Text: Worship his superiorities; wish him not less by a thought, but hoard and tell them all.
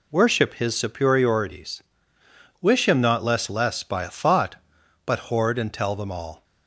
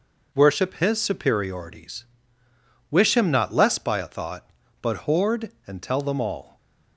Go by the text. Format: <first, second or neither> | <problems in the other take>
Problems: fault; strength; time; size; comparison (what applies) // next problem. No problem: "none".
second | says "less" twice; at 3.4 s